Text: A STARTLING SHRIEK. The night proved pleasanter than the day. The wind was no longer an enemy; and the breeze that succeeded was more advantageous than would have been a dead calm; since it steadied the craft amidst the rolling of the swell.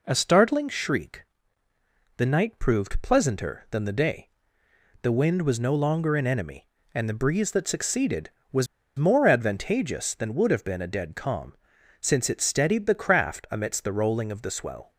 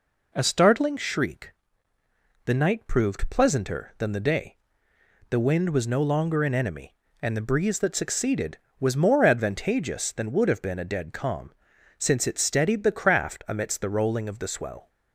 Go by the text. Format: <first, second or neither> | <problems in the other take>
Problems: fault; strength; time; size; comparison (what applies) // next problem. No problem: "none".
second | pauses between "was" and "more"; slight; at 8.6 s; 0.31 s long